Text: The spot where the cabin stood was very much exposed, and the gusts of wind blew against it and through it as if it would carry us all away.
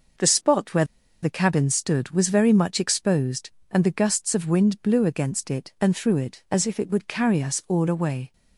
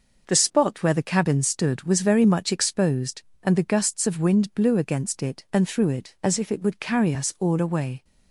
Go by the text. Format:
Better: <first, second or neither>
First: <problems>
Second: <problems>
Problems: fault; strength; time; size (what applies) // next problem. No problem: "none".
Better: second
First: pauses between "where" and "the"; at 0.8 s; 0.38 s long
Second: none